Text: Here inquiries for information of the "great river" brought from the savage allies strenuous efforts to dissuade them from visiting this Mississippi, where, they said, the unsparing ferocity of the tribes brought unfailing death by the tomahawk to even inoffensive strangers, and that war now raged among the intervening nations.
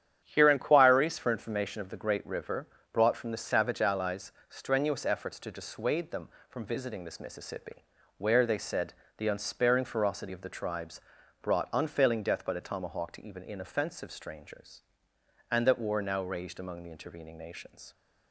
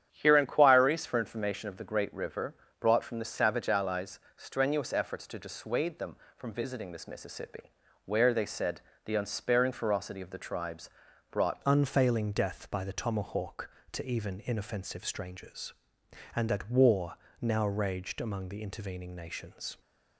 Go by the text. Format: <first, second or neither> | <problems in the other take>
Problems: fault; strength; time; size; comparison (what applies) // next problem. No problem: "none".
first | starts louder than the rest; strong; until 1.1 s; 9.5 dB; strong in the first // pauses between "river" and "brought"; slight; at 2.5 s; 0.26 s long; slight in the first // pauses between "allies" and "strenuous"; slight; at 4.1 s; 0.18 s long; slight in the first // pauses between "tribes" and "brought"; at 10.8 s; 0.40 s long; also in the first // changes voice at "unfailing"; from 11.6 s on; 8.1 s long // pauses between "war" and "now"; slight; at 17.1 s; 0.24 s long